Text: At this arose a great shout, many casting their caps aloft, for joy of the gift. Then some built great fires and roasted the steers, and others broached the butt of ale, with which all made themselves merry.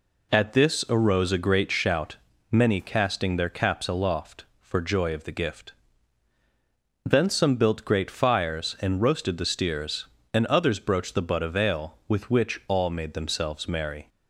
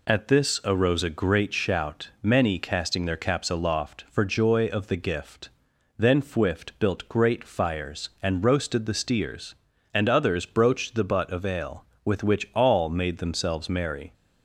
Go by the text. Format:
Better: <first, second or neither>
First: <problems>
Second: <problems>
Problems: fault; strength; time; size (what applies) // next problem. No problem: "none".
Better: first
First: none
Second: says "fwift" for "some"; at 6.2 s